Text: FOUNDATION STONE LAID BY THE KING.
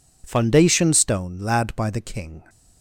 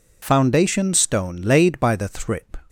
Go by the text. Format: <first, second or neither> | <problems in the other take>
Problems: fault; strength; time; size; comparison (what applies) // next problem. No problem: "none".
first | says "Thrip" for "KING"; at 2.0 s